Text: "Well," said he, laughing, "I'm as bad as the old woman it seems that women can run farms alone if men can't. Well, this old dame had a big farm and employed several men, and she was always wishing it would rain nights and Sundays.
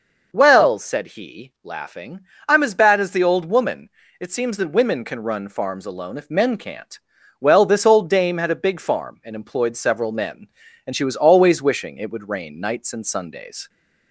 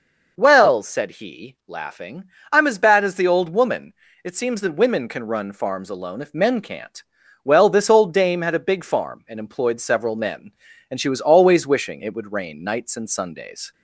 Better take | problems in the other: neither | pauses between "woman" and "it"; slight; the same in both

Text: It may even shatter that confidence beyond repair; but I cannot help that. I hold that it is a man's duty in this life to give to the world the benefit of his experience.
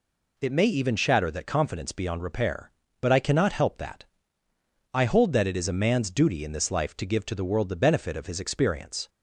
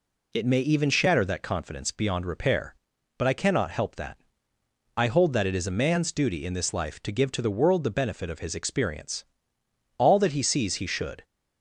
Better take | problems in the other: first | goes on to say "All that he sees he should"; noticeable; from 9.9 s on; 1.2 s long

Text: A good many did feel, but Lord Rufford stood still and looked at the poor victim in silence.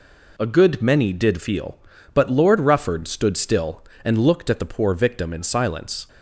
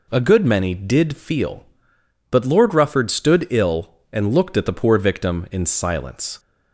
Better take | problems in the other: first | says "ill" for "still"; at 3.4 s

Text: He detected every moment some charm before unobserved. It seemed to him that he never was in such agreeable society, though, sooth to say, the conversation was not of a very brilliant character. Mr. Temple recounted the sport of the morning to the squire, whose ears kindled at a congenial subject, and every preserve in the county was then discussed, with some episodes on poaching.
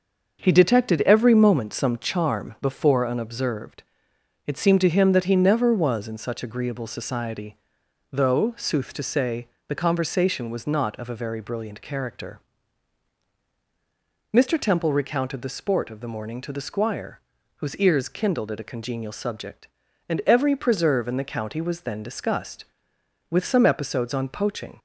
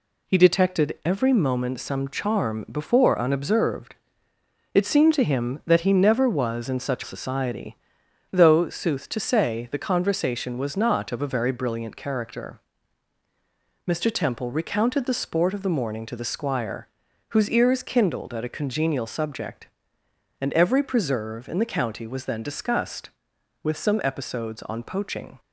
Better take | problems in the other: first | skips "agreeable"; at 7.0 s

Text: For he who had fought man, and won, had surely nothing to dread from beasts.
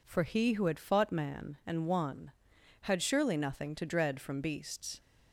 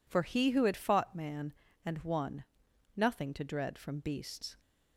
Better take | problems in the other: first | skips "had surely"; at 2.7 s

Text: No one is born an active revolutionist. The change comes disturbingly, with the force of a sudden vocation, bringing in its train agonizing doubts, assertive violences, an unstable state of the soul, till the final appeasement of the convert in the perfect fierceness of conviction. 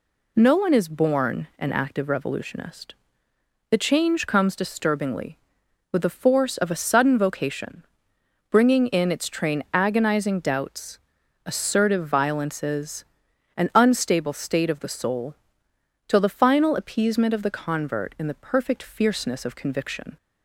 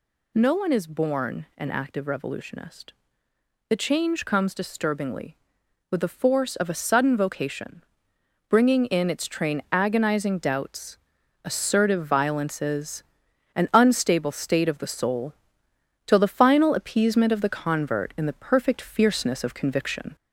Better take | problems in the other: first | gets louder; slight; throughout; 2.5 dB

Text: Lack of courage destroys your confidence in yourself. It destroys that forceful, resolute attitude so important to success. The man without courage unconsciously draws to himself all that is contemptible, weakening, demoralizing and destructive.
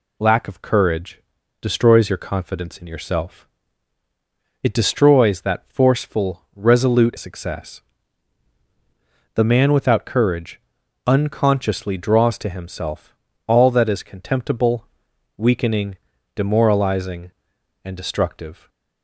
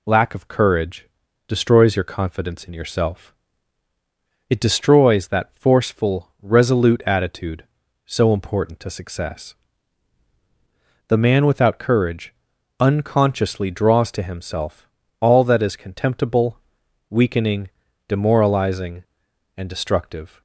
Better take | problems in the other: second | pauses between "courage" and "destroys"; at 1.2 s; 0.40 s long; also in the second // skips "attitude so important to"; at 7.1 s // pauses between "courage" and "unconsciously"; noticeable; at 10.6 s; 0.46 s long; noticeable in the second // pauses between "himself" and "all"; slight; at 13.1 s; 0.32 s long; slight in the second

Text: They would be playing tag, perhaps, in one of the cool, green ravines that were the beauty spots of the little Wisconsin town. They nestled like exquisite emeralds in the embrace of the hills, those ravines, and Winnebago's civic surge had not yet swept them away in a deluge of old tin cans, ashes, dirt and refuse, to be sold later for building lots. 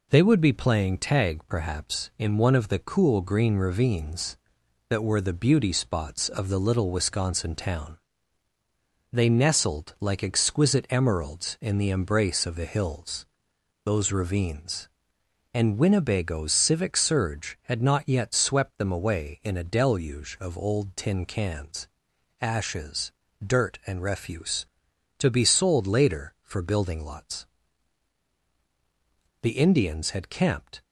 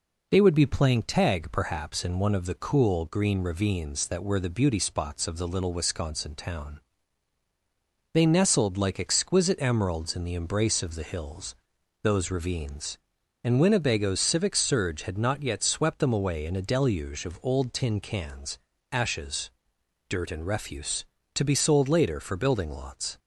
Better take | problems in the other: second | goes on to say "The Indians had camped"; from 29.4 s on; 1.4 s long

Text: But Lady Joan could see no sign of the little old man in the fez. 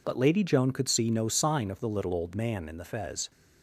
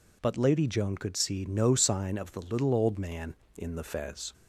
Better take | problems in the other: neither | none

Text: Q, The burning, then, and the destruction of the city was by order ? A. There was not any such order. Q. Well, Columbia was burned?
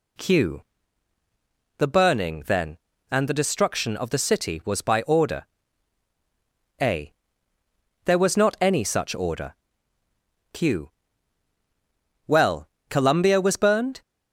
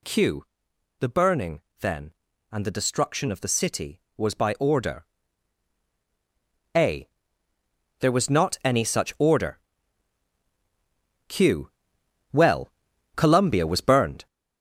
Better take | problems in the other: first | gets louder; noticeable; throughout; 5.5 dB

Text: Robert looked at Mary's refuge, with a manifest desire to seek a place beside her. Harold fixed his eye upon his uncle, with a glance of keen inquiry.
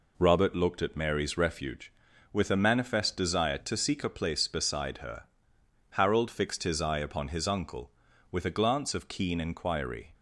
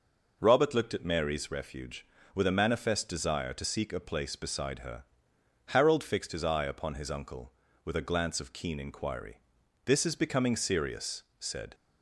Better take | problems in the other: first | goes on to say "This is becoming serious said"; strong; from 9.8 s on; 1.8 s long

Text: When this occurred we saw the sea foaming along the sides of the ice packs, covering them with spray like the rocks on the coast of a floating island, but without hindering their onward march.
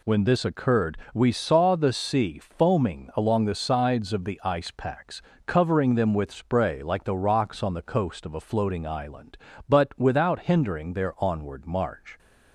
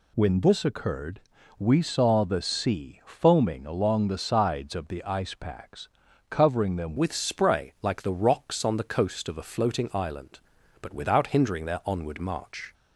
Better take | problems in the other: first | pauses between "occurred" and "we"; at 1.1 s; 0.40 s long; slight in the first // changes voice at "with"; from 6.9 s on; 5.8 s long

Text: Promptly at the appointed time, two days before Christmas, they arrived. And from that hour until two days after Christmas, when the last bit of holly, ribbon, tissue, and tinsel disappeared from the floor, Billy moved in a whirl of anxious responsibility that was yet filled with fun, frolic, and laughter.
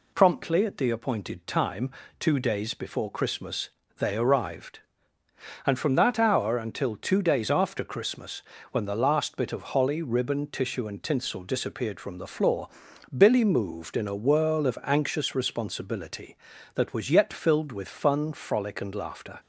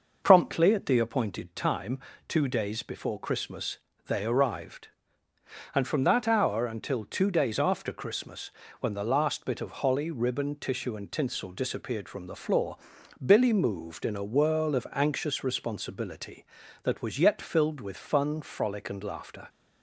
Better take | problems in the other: first | starts louder than the rest; noticeable; until 1.5 s; 5.5 dB

